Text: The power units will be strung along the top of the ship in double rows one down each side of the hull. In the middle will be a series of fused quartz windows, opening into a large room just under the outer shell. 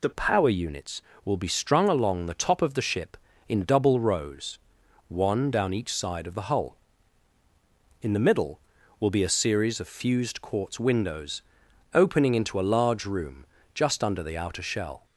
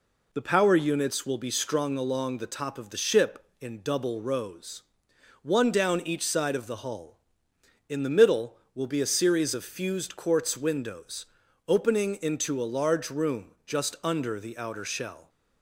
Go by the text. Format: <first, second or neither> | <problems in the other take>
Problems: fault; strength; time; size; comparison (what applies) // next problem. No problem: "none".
second | changes voice at "power"; from 0.1 s on; 14.9 s long // pauses between "rows" and "one"; noticeable; at 4.5 s; 0.52 s long; noticeable in the second // pauses between "room" and "just"; slight; at 13.4 s; 0.28 s long